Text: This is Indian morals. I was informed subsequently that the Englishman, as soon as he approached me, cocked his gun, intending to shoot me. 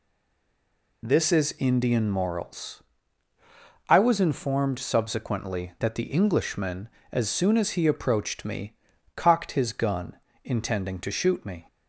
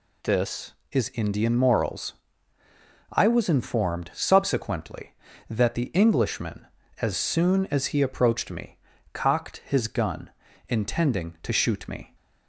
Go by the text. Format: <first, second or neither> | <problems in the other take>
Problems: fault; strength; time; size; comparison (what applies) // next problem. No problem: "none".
second | stays silent before the first word; until 1.0 s; 1.0 s long